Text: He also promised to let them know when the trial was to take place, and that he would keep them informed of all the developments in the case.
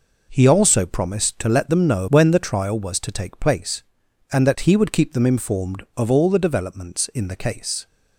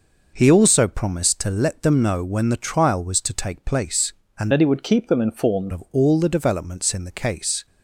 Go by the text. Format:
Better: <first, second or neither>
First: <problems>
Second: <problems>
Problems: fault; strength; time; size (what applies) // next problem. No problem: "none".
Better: first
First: none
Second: changes voice from "that" to "informed"; from 4.5 to 5.7 s; 1.2 s long